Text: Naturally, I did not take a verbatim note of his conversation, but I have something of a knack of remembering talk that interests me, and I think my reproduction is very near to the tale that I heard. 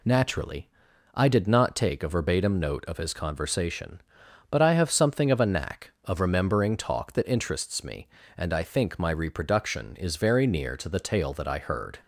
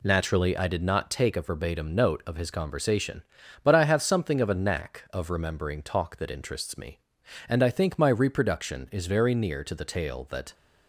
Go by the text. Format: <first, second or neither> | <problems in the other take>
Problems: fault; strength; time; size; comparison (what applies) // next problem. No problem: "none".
first | stops before "I heard"; at 10.5 s